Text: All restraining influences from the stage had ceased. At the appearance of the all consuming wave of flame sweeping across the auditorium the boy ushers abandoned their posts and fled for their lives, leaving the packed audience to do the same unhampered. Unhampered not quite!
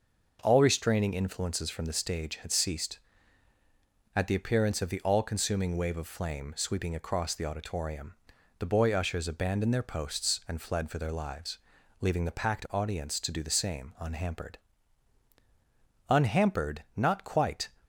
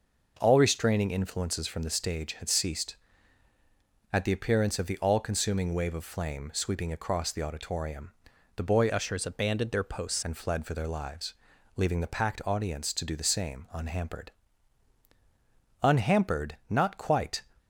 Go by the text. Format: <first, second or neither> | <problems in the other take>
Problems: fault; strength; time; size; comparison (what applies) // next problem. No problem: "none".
first | pauses between "auditorium" and "the"; at 8.1 s; 0.44 s long; also in the first // changes voice from "ushers" to "posts"; from 8.8 to 10.2 s; 1.4 s long